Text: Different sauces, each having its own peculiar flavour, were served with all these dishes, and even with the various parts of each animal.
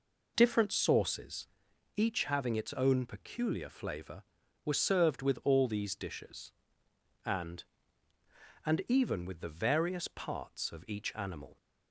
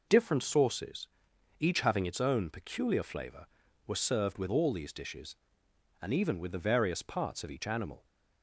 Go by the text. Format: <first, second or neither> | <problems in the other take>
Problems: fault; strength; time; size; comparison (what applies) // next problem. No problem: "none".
second | says "and" twice; at 8.6 s